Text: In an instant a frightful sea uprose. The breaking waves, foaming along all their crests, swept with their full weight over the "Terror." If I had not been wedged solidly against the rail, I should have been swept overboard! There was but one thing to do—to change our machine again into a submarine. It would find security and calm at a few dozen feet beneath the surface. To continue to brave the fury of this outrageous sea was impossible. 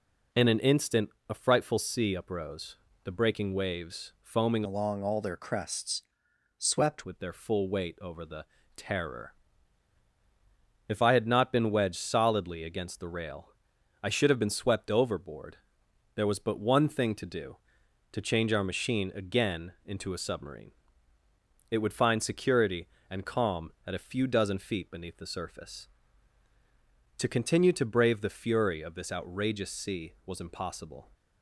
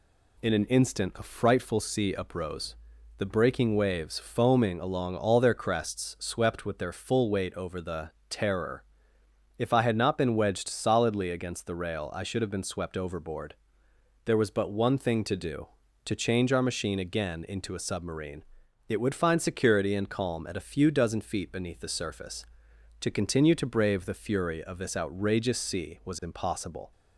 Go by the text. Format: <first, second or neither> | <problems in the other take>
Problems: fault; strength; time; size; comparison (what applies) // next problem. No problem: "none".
second | pauses between "instant" and "a"; slight; at 1.0 s; 0.18 s long // changes voice from "along" to "swept"; from 4.6 to 7.0 s; 2.4 s long // pauses between "the" and "Terror"; slight; at 8.4 s; 0.32 s long; slight in the second